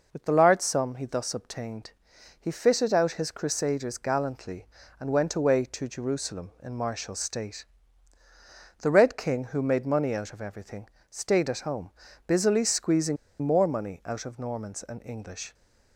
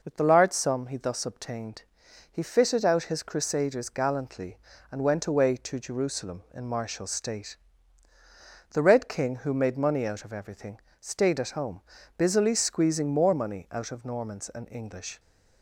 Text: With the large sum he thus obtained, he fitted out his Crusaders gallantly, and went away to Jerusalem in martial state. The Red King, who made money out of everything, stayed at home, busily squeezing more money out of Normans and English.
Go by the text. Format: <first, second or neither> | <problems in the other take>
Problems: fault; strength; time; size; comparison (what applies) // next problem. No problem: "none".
second | pauses between "squeezing" and "more"; slight; at 13.1 s; 0.25 s long